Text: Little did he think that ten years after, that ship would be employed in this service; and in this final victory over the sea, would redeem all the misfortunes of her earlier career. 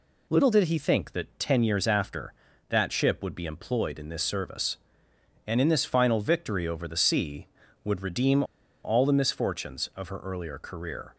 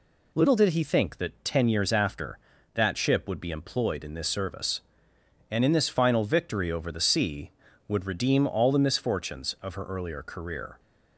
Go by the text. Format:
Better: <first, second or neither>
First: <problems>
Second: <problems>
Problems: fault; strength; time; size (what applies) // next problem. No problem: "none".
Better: second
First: pauses between "redeem" and "all"; at 8.4 s; 0.40 s long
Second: none